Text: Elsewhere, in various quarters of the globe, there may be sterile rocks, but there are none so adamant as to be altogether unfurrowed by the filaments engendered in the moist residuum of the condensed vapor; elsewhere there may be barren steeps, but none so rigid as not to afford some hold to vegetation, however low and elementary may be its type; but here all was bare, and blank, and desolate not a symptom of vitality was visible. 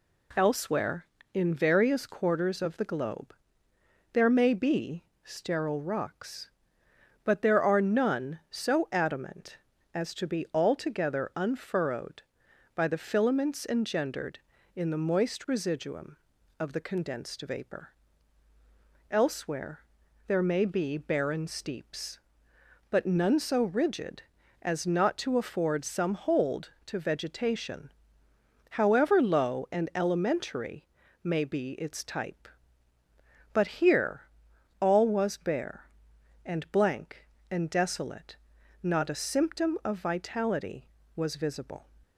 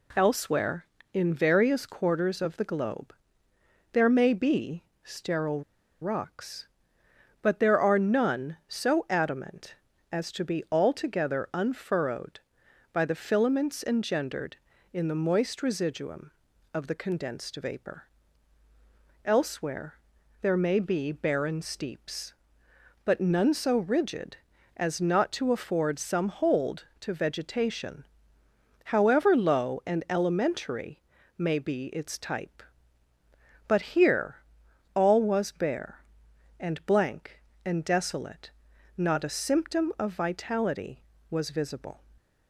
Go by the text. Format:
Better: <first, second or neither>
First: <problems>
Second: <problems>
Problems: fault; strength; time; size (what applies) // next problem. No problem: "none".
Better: first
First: pauses between "be" and "sterile"; slight; at 5.0 s; 0.22 s long // pauses between "elsewhere" and "there"; at 19.8 s; 0.44 s long // pauses between "elementary" and "may"; at 30.8 s; 0.38 s long // pauses between "here" and "all"; noticeable; at 34.2 s; 0.58 s long // pauses between "desolate" and "not"; noticeable; at 38.3 s; 0.48 s long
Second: pauses between "be" and "sterile"; slight; at 4.8 s; 0.22 s long // pauses between "sterile" and "rocks"; at 5.6 s; 0.40 s long // pauses between "elsewhere" and "there"; at 19.9 s; 0.44 s long // pauses between "elementary" and "may"; at 30.9 s; 0.38 s long // pauses between "here" and "all"; noticeable; at 34.3 s; 0.58 s long // pauses between "desolate" and "not"; noticeable; at 38.4 s; 0.48 s long